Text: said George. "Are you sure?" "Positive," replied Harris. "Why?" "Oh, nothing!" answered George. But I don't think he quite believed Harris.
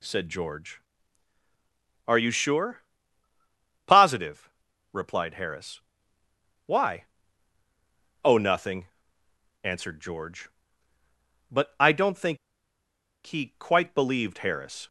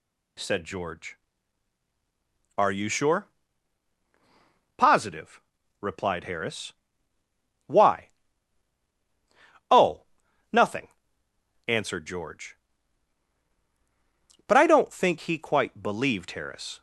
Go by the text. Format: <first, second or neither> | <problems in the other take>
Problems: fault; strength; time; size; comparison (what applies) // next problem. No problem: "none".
second | pauses between "think" and "he"; noticeable; at 12.3 s; 0.89 s long